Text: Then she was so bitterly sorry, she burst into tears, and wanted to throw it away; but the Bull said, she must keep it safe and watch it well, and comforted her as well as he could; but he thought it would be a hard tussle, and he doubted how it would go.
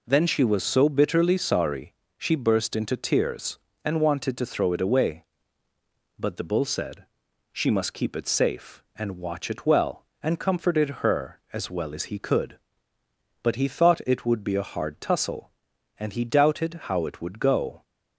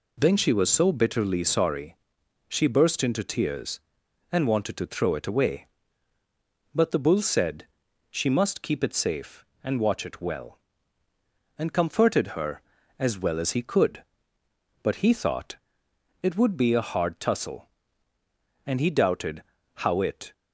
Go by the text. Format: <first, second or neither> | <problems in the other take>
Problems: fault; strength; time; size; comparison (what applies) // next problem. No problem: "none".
first | pauses between "thought" and "it"; noticeable; at 15.5 s; 0.66 s long // pauses between "doubted" and "how"; slight; at 19.4 s; 0.30 s long // stops before "would go"; at 20.3 s